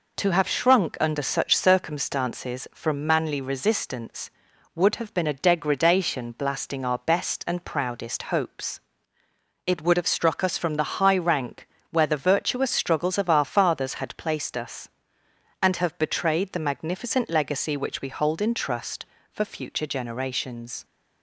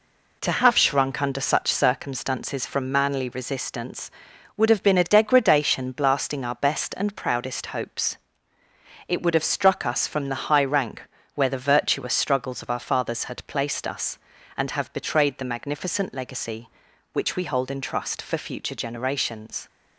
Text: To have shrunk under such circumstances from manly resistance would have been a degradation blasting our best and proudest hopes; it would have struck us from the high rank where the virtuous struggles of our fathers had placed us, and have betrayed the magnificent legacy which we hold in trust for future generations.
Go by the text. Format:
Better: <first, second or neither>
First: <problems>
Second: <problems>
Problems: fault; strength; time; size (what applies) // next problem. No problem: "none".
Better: neither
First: pauses between "rank" and "where"; slight; at 11.6 s; 0.24 s long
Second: pauses between "rank" and "where"; slight; at 11.0 s; 0.32 s long